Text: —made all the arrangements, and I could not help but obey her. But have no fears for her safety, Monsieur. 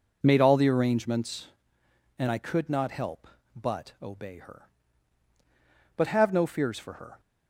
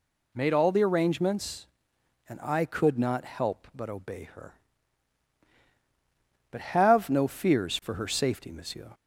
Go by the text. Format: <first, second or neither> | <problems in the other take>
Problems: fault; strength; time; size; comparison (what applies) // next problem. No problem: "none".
second | stops before "safety Monsieur"; at 7.1 s